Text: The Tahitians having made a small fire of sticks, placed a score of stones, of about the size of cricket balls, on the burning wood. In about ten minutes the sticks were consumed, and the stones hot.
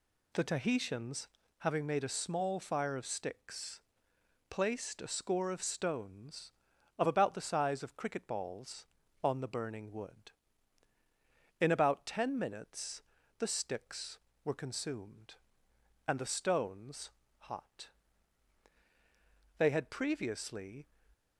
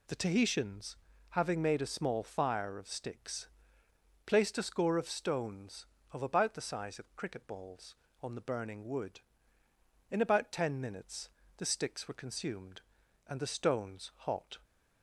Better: second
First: pauses between "Tahitians" and "having"; slight; at 1.2 s; 0.30 s long // pauses between "minutes" and "the"; slight; at 13.0 s; 0.36 s long // pauses between "stones" and "hot"; slight; at 17.1 s; 0.34 s long // goes on to say "They had previously"; noticeable; from 19.5 s on; 1.2 s long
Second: pauses between "Tahitians" and "having"; slight; at 0.9 s; 0.32 s long // pauses between "minutes" and "the"; slight; at 11.3 s; 0.26 s long

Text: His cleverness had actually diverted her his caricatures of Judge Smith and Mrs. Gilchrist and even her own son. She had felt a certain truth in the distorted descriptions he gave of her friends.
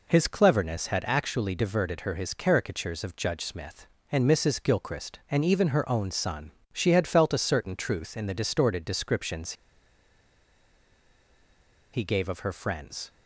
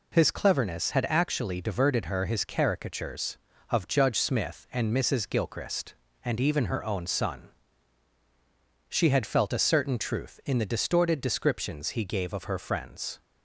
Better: second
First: pauses between "descriptions" and "he"; strong; at 9.5 s; 2.4 s long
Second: none

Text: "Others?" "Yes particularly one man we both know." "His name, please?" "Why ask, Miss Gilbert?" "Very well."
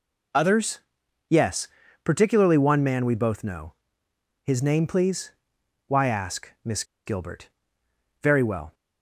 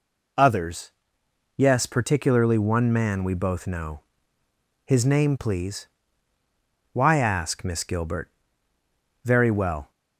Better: second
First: pauses between "Yes" and "particularly"; slight; at 1.6 s; 0.36 s long // pauses between "Miss" and "Gilbert"; slight; at 6.8 s; 0.22 s long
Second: none

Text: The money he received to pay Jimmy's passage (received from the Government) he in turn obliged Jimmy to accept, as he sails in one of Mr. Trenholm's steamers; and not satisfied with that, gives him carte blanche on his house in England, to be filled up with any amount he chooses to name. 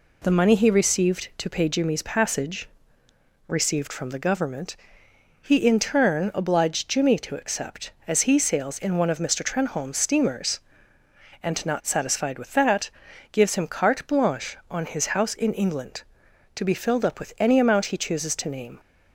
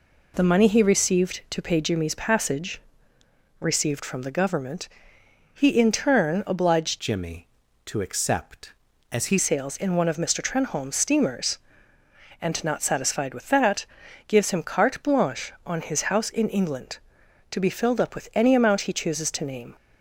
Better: first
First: none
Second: changes voice from "Jimmy" to "he"; from 6.9 to 9.3 s; 2.4 s long

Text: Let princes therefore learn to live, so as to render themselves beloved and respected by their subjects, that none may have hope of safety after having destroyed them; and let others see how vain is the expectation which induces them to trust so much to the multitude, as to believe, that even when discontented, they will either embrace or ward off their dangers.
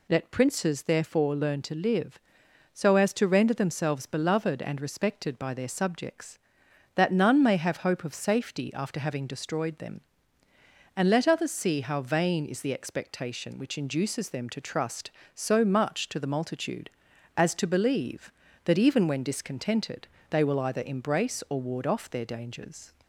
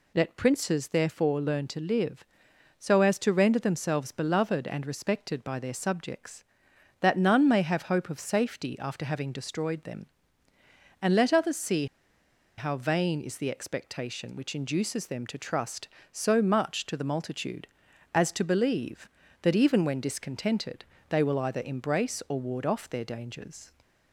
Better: first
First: none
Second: pauses between "see" and "how"; noticeable; at 11.8 s; 0.72 s long

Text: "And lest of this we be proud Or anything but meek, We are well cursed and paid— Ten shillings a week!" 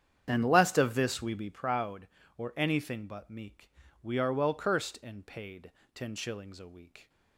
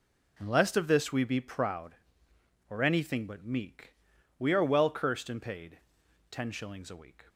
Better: second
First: starts louder than the rest; strong; until 1.7 s; 8.5 dB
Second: none

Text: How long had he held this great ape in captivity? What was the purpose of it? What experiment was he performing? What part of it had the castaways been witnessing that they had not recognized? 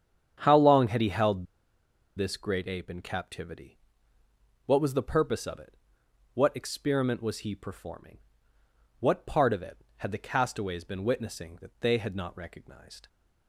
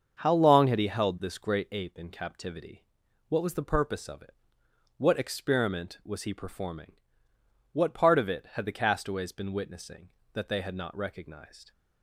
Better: second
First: starts louder than the rest; strong; until 1.4 s; 8.5 dB // pauses between "held" and "this"; noticeable; at 1.4 s; 0.72 s long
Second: starts louder than the rest; until 1.2 s; 6.5 dB

